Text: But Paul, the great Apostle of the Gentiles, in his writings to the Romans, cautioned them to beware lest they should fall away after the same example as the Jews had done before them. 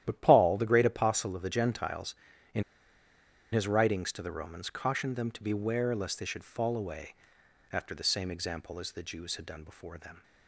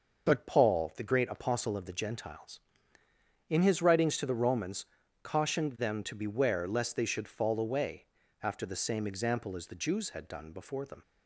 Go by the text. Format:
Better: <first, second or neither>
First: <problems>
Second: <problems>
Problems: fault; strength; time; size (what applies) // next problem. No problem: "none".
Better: second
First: starts louder than the rest; strong; until 1.0 s; 11.5 dB // pauses between "in" and "his"; noticeable; at 2.6 s; 0.91 s long // pauses between "away" and "after"; noticeable; at 7.1 s; 0.56 s long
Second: starts louder than the rest; noticeable; until 1.3 s; 6 dB // pauses between "away" and "after"; at 8.0 s; 0.38 s long